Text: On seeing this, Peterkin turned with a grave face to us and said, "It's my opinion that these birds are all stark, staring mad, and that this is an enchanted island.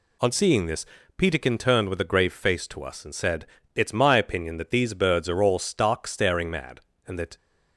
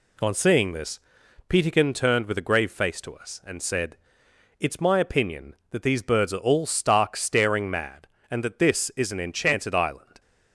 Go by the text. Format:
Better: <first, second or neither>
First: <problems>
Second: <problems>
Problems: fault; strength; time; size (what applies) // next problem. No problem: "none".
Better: second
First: stops before "this is an enchanted island"; at 7.3 s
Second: none